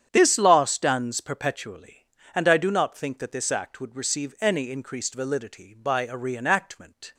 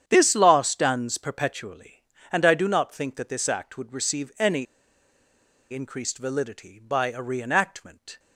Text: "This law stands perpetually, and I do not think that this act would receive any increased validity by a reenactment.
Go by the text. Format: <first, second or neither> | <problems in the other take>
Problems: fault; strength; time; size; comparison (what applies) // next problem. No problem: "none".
first | starts louder than the rest; strong; until 1.0 s; 9 dB; strong in the first // pauses between "any" and "increased"; at 4.6 s; 1.0 s long